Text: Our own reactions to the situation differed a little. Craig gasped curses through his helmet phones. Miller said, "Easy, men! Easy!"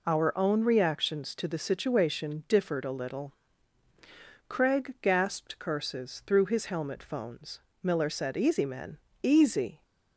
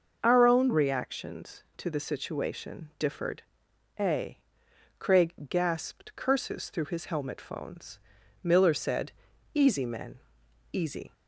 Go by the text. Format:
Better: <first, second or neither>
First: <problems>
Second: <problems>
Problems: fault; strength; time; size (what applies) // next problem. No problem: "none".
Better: first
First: none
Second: starts louder than the rest; noticeable; until 1.2 s; 6 dB // pauses between "differed" and "a"; noticeable; at 3.4 s; 0.58 s long // skips "little"; at 4.6 s // pauses between "Craig" and "gasped"; slight; at 5.3 s; 0.16 s long